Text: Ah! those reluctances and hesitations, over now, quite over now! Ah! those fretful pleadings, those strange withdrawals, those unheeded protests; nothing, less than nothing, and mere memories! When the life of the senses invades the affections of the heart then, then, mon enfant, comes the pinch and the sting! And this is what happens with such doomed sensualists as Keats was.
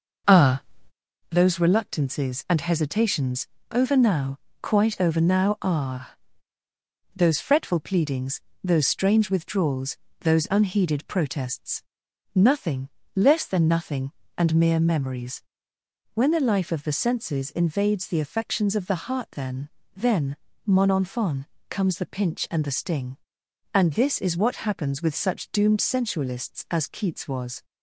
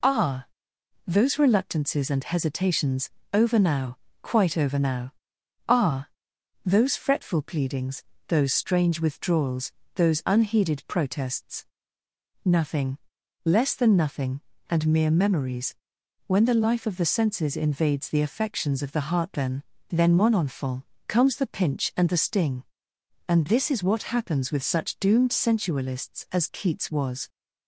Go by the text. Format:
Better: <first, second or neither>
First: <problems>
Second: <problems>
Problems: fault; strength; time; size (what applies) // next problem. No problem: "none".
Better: second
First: starts louder than the rest; noticeable; until 1.3 s; 6 dB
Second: none